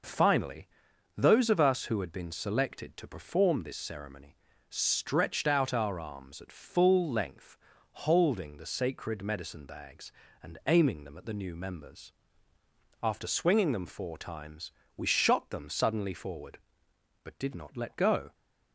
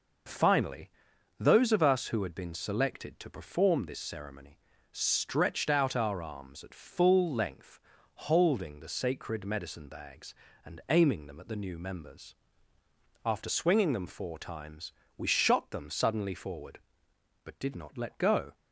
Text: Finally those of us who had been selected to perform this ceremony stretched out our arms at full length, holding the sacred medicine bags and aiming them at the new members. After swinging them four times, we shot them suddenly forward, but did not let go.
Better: neither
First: pauses between "Finally" and "those"; noticeable; at 0.6 s; 0.50 s long // pauses between "ceremony" and "stretched"; slight; at 4.3 s; 0.32 s long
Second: pauses between "Finally" and "those"; noticeable; at 0.8 s; 0.50 s long // pauses between "ceremony" and "stretched"; slight; at 4.5 s; 0.32 s long

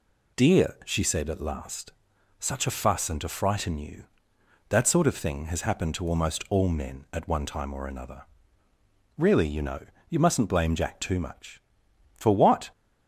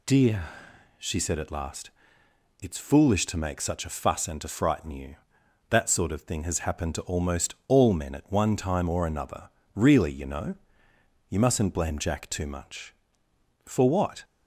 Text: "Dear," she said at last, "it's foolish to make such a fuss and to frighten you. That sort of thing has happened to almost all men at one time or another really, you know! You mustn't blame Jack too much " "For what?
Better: second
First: skips "it's foolish to make"; at 2.1 s // pauses between "another" and "really"; noticeable; at 8.2 s; 0.92 s long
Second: pauses between "another" and "really"; slight; at 9.4 s; 0.26 s long

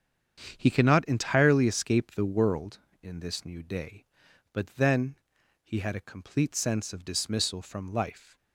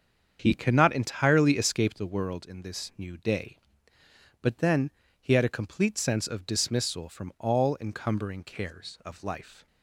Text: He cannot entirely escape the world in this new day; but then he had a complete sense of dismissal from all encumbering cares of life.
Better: second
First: starts louder than the rest; strong; until 1.5 s; 8 dB // pauses between "then" and "he"; noticeable; at 5.1 s; 0.48 s long // skips "all encumbering cares of"; at 7.9 s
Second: starts louder than the rest; strong; until 1.4 s; 7 dB // pauses between "then" and "he"; slight; at 4.9 s; 0.30 s long

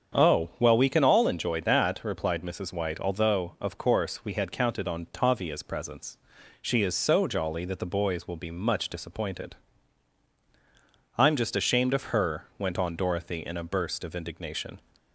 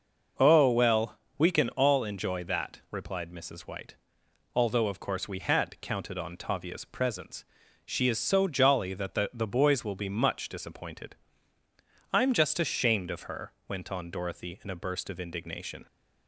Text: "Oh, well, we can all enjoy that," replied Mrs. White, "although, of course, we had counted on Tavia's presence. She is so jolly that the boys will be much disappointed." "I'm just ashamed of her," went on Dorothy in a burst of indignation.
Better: first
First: starts louder than the rest; strong; until 1.2 s; 7.5 dB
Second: starts louder than the rest; noticeable; until 1.6 s; 6 dB // says "the" twice; at 9.3 s

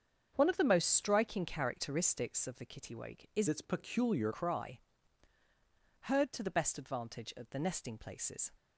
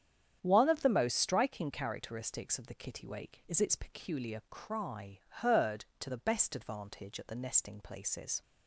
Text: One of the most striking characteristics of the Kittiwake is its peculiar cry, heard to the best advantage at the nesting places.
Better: second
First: starts louder than the rest; strong; until 1.3 s; 7.5 dB // changes voice from "its" to "peculiar"; from 3.4 to 4.3 s; 0.9 s long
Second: starts louder than the rest; strong; until 1.4 s; 9 dB

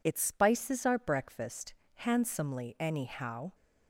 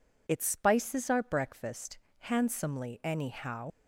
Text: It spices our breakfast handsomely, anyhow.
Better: first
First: pauses between "breakfast" and "handsomely"; slight; at 1.7 s; 0.22 s long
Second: pauses between "breakfast" and "handsomely"; slight; at 1.9 s; 0.22 s long // leaves "anyhow" unfinished; at 3.7 s; 85 ms

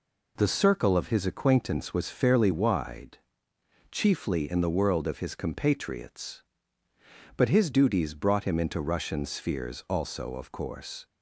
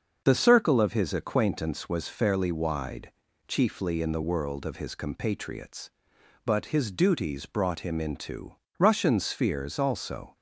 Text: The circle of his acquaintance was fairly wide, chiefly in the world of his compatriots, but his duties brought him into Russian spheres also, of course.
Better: first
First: none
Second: starts louder than the rest; until 1.2 s; 6.5 dB // pauses between "into" and "Russian"; slight; at 8.5 s; 0.22 s long // stops before "of course"; at 10.3 s

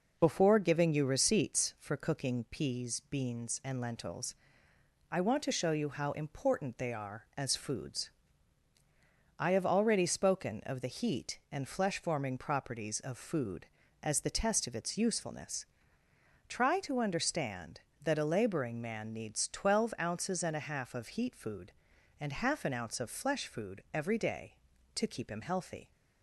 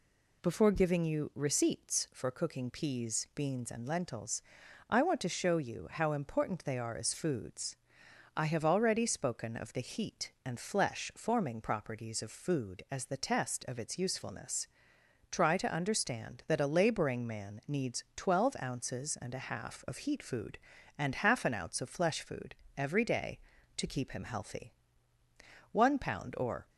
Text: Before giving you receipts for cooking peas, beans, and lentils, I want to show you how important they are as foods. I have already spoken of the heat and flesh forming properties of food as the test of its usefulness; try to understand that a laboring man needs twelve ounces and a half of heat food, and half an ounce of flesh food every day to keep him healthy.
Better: first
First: none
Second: pauses between "food" and "every"; slight; at 22.5 s; 0.22 s long // goes on to say "One pound or"; noticeable; from 25.7 s on; 0.96 s long

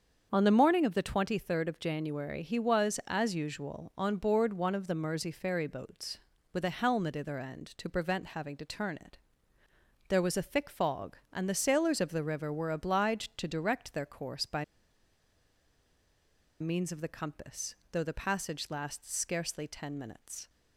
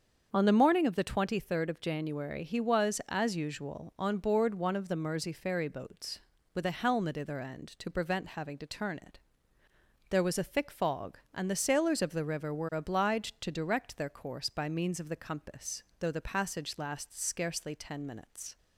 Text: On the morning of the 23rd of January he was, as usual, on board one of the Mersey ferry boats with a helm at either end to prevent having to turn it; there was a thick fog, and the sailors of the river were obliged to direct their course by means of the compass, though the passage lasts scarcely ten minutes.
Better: second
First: starts louder than the rest; until 1.3 s; 7 dB // pauses between "by" and "means"; strong; at 14.6 s; 1.9 s long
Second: starts louder than the rest; until 1.3 s; 7 dB

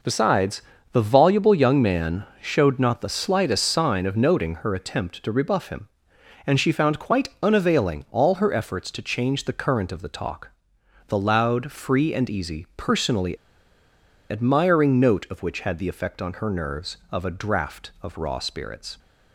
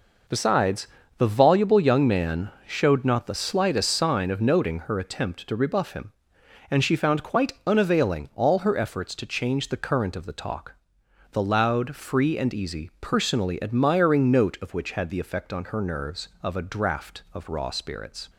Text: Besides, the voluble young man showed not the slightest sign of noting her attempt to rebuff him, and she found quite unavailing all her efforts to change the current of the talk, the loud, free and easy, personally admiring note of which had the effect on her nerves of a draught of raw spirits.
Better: second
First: pauses between "man" and "showed"; slight; at 2.2 s; 0.18 s long // pauses between "personally" and "admiring"; noticeable; at 13.3 s; 0.93 s long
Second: pauses between "man" and "showed"; slight; at 2.4 s; 0.18 s long

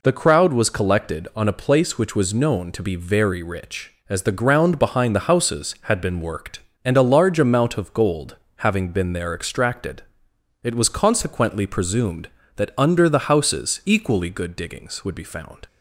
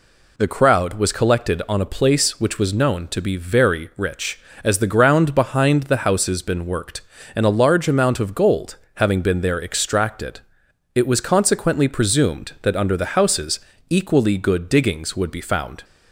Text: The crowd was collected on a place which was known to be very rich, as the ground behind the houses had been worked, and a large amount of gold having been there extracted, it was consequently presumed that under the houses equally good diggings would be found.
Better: first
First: pauses between "gold" and "having"; slight; at 8.3 s; 0.20 s long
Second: skips "had"; at 6.4 s // pauses between "gold" and "having"; slight; at 8.7 s; 0.20 s long // pauses between "houses" and "equally"; slight; at 13.5 s; 0.30 s long

